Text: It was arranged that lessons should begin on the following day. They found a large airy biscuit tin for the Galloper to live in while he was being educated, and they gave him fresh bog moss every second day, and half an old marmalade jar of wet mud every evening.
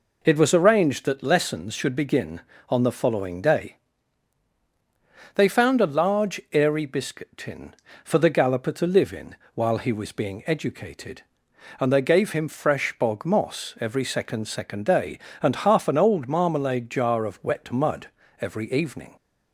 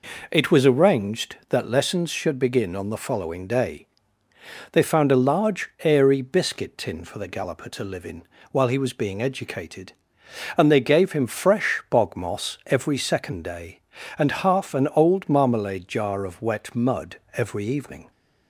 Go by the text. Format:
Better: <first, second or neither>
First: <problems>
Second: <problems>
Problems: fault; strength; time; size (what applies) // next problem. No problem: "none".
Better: second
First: pauses between "in" and "while"; slight; at 9.3 s; 0.18 s long // says "second" twice; at 14.4 s // pauses between "mud" and "every"; slight; at 18.0 s; 0.32 s long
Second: pauses between "in" and "while"; slight; at 8.2 s; 0.26 s long // pauses between "mud" and "every"; slight; at 17.1 s; 0.16 s long